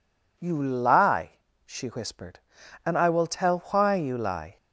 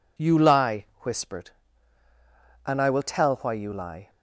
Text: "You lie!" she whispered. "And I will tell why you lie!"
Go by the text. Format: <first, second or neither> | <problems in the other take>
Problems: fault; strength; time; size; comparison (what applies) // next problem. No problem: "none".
first | skips "she"; at 0.9 s